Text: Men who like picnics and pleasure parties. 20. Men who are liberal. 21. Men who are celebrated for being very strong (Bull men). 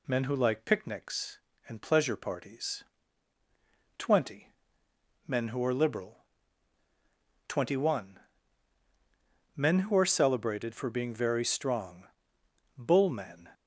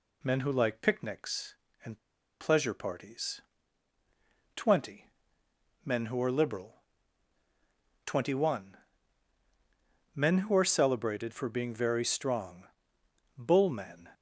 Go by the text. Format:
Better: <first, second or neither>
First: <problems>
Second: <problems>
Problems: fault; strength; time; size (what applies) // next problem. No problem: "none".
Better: first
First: none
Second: pauses between "and" and "pleasure"; at 1.9 s; 0.43 s long